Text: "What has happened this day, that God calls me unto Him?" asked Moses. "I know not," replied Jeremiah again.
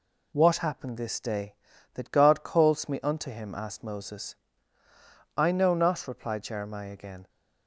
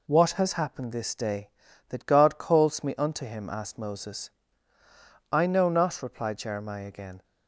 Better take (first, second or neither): second